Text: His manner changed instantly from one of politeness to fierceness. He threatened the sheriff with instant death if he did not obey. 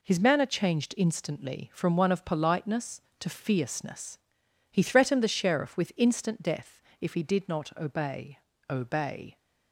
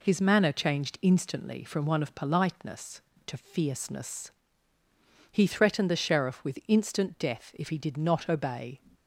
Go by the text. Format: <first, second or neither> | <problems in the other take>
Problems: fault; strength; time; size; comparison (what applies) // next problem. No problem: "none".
second | pauses between "death" and "if"; slight; at 6.8 s; 0.18 s long // says "obey" twice; at 8.6 s